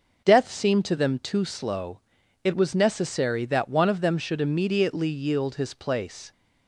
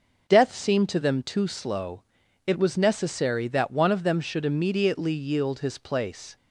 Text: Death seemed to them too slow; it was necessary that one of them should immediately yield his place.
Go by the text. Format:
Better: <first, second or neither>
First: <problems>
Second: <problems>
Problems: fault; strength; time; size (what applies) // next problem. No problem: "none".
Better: neither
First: none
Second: none